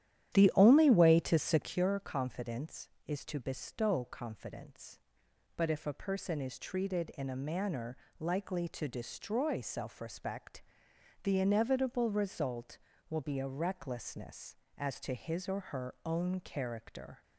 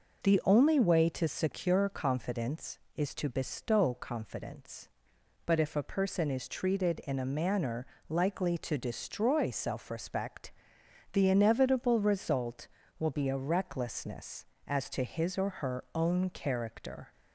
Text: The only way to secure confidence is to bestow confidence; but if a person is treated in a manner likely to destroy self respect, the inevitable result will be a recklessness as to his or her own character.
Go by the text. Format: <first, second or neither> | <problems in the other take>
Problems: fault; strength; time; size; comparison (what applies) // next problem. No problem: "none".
second | starts louder than the rest; strong; until 1.9 s; 11 dB // pauses between "manner" and "likely"; slight; at 7.9 s; 0.20 s long; slight in the second